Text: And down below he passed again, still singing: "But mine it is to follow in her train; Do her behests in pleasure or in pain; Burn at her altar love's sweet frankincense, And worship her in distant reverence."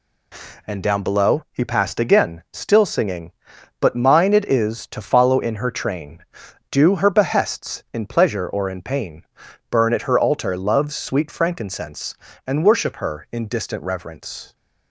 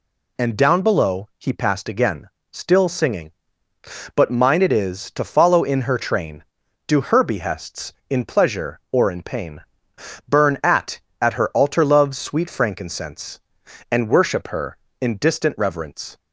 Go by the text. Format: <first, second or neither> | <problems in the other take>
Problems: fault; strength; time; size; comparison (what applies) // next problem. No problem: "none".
first | says "at" twice; at 11.2 s